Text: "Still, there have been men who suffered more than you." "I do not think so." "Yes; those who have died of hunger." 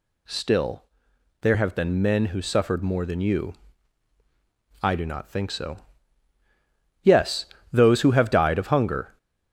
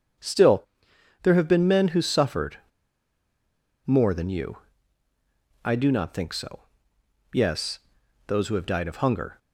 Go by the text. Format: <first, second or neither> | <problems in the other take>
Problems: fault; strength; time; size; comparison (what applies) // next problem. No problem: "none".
first | starts louder than the rest; strong; until 1.7 s; 7 dB // pauses between "suffered" and "more"; strong; at 2.5 s; 1.3 s long